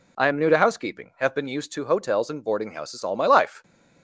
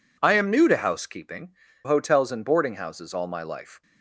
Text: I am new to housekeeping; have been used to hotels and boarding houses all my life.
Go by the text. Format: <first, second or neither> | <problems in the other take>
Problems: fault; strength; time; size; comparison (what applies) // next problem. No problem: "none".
first | skips "have been used to"; at 1.6 s